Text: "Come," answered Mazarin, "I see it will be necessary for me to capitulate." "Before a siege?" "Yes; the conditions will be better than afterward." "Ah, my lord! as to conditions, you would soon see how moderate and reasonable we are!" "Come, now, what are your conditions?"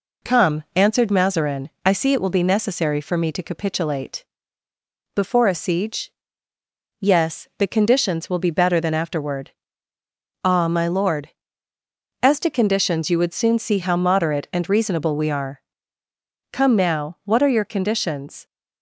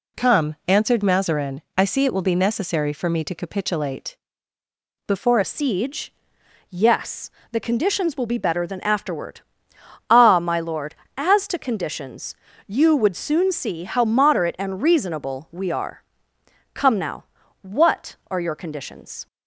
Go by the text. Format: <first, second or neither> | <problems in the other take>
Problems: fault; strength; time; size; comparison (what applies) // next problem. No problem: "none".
first | changes voice at "a"; from 5.4 s on; 13.8 s long